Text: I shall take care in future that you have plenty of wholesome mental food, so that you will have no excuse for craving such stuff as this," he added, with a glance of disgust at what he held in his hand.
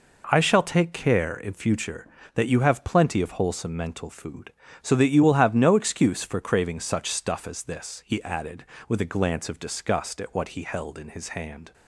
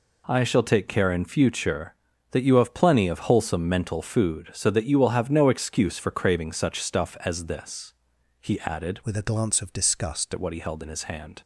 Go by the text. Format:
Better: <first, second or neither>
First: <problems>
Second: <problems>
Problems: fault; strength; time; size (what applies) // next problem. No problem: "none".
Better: first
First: none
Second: changes voice from "with" to "disgust"; from 9.0 to 10.3 s; 1.3 s long